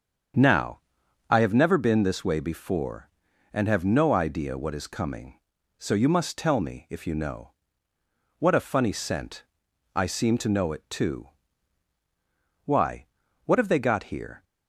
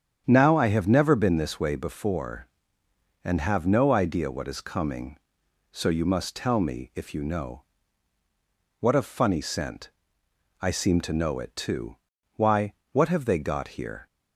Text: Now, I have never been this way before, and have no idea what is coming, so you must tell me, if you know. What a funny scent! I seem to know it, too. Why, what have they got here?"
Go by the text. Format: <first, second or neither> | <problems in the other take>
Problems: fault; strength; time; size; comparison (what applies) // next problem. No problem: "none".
neither | starts louder than the rest; strong; the same in both